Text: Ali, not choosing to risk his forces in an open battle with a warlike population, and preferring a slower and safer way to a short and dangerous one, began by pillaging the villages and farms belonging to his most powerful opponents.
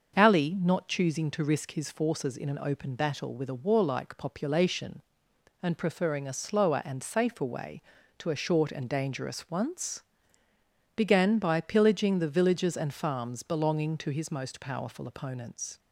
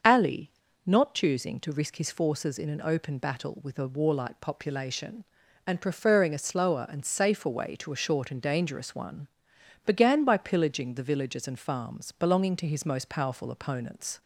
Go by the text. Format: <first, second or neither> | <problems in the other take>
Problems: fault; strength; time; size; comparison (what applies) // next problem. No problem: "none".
second | starts louder than the rest; until 1.2 s; 6.5 dB; also in the second // says "once" for "one"; at 9.5 s